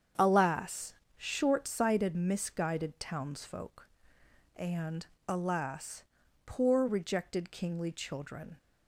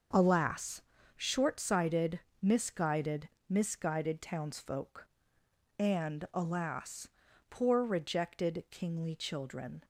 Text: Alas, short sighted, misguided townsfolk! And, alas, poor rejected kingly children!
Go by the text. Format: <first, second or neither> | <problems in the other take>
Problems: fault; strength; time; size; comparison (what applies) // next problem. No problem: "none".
first | starts louder than the rest; until 1.4 s; 6.5 dB; strong in the first // says "misguided" twice; at 3.4 s